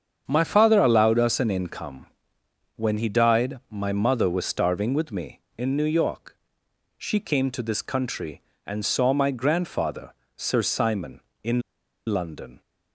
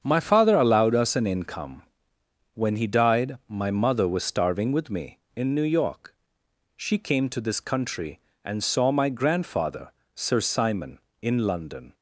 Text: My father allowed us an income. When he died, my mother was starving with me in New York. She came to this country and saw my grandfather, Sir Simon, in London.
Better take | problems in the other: second | starts louder than the rest; strong; until 1.2 s; 7.5 dB; strong in the second // pauses between "in" and "London"; noticeable; at 11.5 s; 0.47 s long

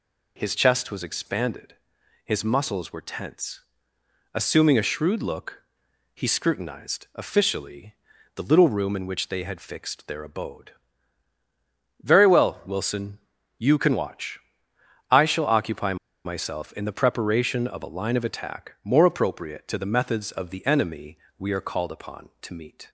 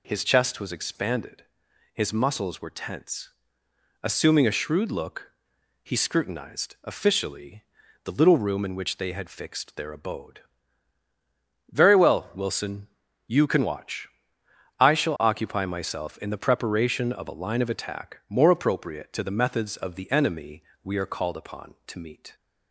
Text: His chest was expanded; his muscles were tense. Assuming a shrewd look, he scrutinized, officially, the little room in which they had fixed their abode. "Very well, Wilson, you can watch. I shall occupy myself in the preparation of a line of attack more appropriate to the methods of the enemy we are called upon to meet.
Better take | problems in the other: second | pauses between "occupy" and "myself"; slight; at 15.9 s; 0.30 s long // pauses between "enemy" and "we"; slight; at 21.1 s; 0.20 s long; slight in the second

